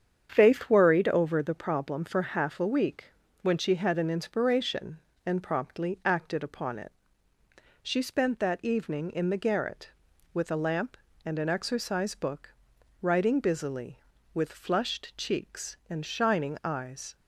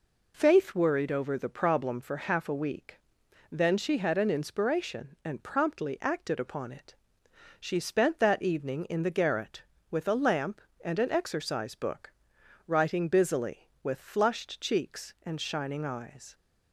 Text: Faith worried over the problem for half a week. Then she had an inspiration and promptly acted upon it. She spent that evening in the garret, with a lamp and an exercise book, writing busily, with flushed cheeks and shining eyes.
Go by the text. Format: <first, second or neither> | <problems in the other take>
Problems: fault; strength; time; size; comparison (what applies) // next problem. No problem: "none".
second | starts louder than the rest; strong; until 1.3 s; 8 dB // says "When" for "Then"; at 3.4 s